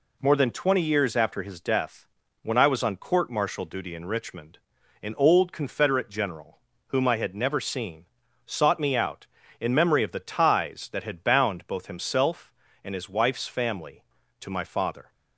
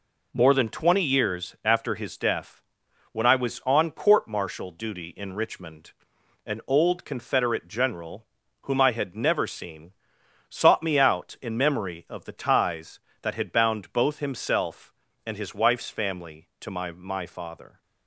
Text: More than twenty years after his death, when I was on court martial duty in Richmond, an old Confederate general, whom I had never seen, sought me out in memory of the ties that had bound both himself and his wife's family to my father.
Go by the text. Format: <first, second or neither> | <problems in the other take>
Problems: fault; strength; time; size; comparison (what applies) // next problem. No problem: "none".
first | says "my" twice; at 16.9 s